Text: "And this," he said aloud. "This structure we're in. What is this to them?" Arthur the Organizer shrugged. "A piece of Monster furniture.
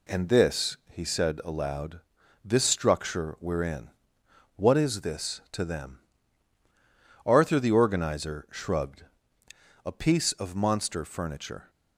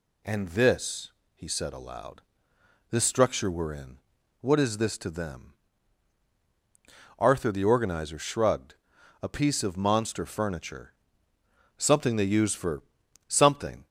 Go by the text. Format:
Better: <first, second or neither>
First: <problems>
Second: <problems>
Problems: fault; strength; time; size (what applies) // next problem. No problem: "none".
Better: first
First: none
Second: goes on to say "Something they use for something"; strong; from 11.7 s on; 2.1 s long